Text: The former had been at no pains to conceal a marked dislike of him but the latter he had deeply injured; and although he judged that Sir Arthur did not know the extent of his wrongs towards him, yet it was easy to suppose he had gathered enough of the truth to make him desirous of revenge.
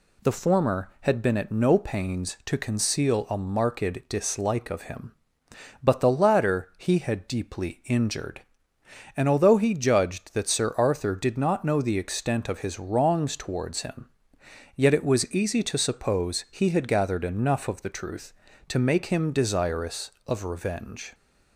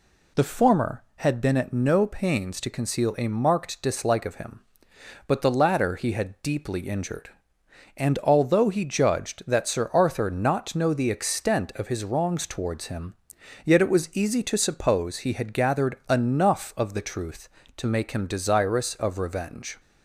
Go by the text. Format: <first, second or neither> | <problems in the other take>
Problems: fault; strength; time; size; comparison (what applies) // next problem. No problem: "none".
first | skips "did"; at 10.2 s